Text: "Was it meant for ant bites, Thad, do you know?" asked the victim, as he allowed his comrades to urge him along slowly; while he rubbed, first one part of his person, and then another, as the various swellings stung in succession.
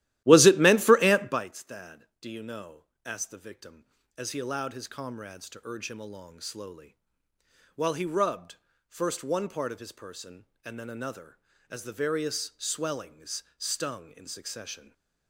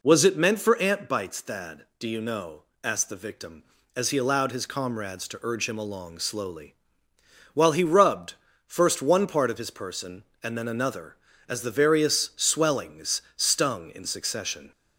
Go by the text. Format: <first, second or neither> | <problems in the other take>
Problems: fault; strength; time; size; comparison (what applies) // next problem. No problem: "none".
second | starts louder than the rest; strong; until 1.5 s; 15 dB // stays silent after the last word; slight; from 14.7 s on; 0.5 s long